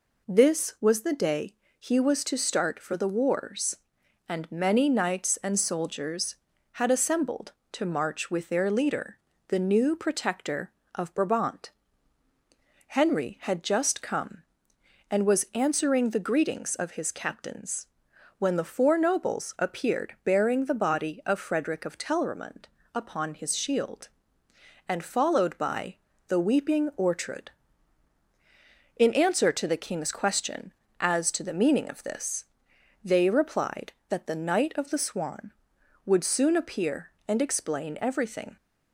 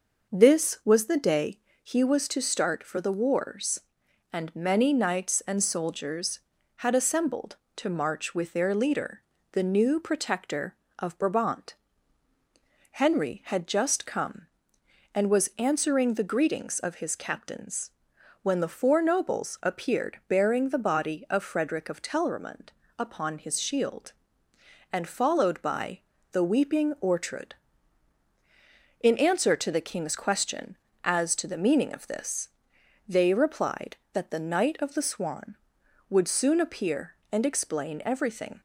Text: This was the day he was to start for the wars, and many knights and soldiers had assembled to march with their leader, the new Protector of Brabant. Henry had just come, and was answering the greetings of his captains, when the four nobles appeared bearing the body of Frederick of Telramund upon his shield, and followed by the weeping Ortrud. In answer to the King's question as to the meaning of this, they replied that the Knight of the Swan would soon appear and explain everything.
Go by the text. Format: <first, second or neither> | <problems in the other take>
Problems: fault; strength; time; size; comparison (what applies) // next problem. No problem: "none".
first | starts louder than the rest; noticeable; until 2.0 s; 6 dB // pauses between "day" and "he"; slight; at 1.5 s; 0.24 s long; slight in the first // pauses between "Telramund" and "upon"; slight; at 22.7 s; 0.28 s long; slight in the first // pauses between "by" and "the"; slight; at 26.0 s; 0.32 s long; slight in the first